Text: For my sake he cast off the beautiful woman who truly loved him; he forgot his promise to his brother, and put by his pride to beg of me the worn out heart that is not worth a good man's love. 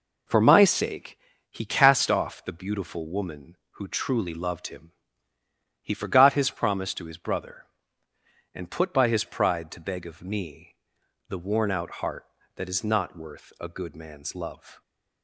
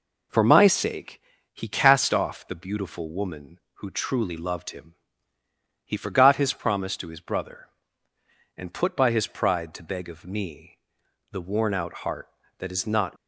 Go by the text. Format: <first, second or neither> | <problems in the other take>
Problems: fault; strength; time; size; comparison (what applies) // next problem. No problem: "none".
first | pauses between "sake" and "he"; slight; at 1.2 s; 0.32 s long; slight in the first // pauses between "me" and "the"; noticeable; at 10.7 s; 0.54 s long; noticeable in the first // stops before "worth a good man's love"; at 13.1 s